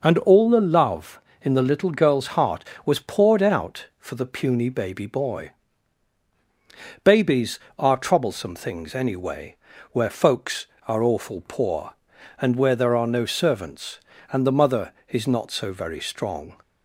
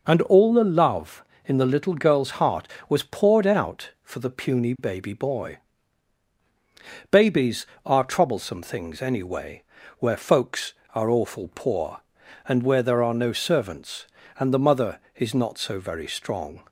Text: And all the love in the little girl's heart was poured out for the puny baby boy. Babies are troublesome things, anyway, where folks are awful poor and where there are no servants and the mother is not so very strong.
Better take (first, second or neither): neither